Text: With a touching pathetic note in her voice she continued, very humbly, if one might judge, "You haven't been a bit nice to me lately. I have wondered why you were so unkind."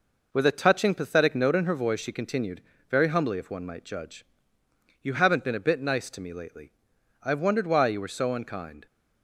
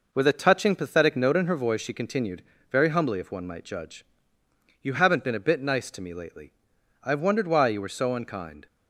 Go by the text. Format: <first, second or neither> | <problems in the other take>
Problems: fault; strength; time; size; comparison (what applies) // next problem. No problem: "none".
neither | none